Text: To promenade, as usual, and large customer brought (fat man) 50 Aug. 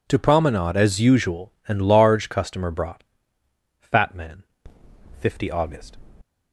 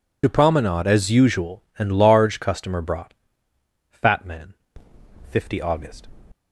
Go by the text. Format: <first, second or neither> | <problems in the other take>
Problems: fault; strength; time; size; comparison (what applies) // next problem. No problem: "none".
first | loses the start of "To"; at 0.2 s; 45 ms